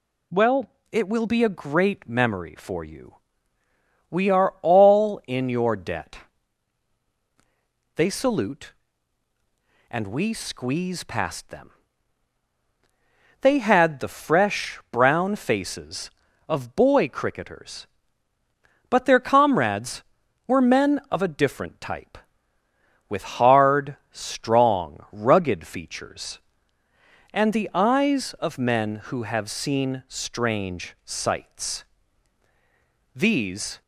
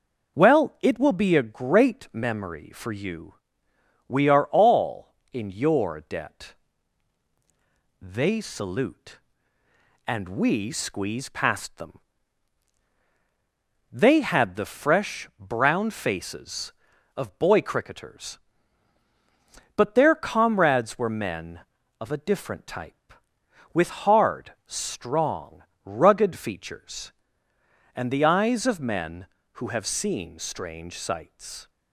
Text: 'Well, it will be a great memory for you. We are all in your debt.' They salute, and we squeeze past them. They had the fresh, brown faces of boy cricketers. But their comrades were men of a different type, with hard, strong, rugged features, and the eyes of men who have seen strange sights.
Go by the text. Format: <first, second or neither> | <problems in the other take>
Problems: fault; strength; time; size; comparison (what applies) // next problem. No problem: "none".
second | goes on to say "These"; noticeable; from 33.1 s on; 0.68 s long